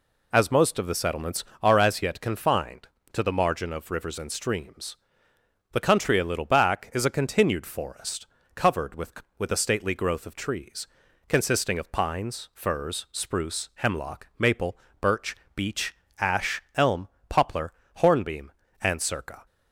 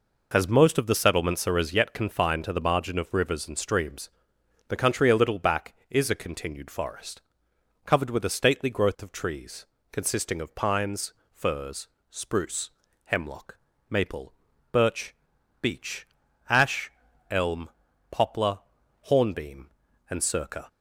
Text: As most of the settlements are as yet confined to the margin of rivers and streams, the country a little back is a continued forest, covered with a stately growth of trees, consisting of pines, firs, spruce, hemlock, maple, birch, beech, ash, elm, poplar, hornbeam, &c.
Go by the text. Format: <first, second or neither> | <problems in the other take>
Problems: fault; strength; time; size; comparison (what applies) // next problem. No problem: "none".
second | says "with" twice; at 9.3 s